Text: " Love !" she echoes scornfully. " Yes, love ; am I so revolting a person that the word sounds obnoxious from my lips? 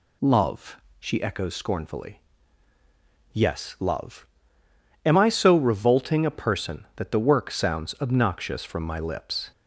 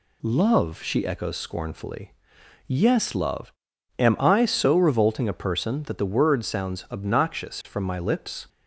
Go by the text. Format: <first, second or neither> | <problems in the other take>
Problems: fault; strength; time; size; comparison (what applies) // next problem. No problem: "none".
second | says "work" for "word"; at 7.2 s